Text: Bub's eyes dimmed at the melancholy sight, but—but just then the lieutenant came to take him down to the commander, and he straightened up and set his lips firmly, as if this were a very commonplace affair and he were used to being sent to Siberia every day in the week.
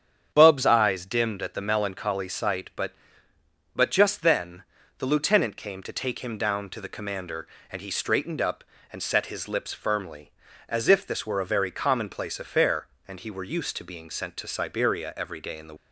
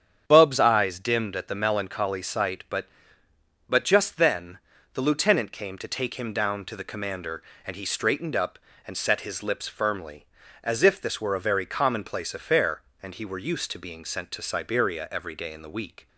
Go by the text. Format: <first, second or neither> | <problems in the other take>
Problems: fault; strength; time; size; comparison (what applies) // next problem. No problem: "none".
second | starts louder than the rest; strong; until 1.3 s; 8 dB; strong in the second // pauses between "then" and "the"; slight; at 4.6 s; 0.36 s long; slight in the second // stops before "week"; at 15.7 s